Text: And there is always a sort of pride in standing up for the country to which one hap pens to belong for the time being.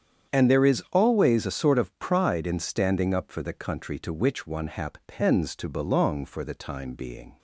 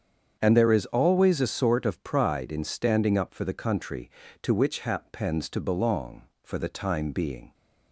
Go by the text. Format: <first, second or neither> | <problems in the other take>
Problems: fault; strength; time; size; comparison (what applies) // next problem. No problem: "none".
first | starts louder than the rest; strong; until 1.4 s; 7.5 dB; strong in the first // skips "one"; at 4.7 s